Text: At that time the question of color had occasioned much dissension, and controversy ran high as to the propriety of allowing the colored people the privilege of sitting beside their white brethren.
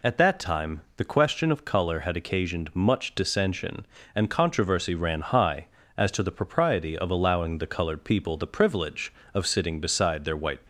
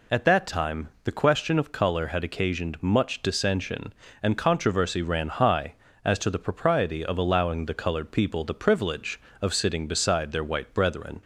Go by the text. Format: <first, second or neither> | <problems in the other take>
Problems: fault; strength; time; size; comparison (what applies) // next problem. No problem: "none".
second | stops before "brethren"; at 10.6 s